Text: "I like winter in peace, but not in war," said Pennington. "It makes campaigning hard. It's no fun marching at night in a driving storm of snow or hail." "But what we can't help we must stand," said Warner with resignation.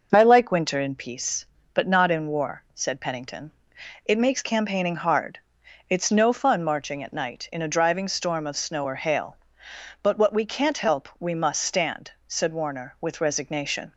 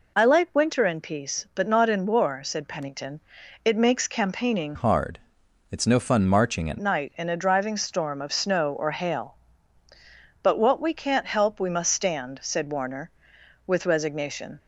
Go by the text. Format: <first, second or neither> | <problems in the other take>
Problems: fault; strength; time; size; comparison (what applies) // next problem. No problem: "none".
first | changes voice from "hard" to "at"; from 4.7 to 6.7 s; 2.0 s long